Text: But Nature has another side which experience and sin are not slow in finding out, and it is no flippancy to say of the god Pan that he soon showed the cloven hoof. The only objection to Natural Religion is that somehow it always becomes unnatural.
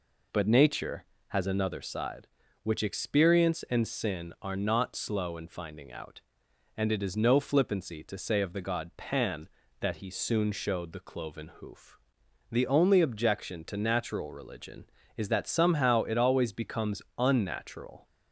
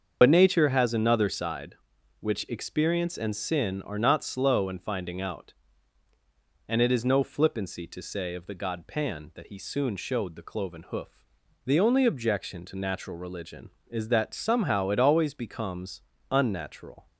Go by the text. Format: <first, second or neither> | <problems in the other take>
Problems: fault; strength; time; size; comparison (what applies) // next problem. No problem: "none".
first | loses the start of "But"; at 0.2 s; 70 ms // starts louder than the rest; until 1.2 s; 7 dB // pauses between "becomes" and "unnatural"; slight; at 16.0 s; 0.30 s long; slight in the first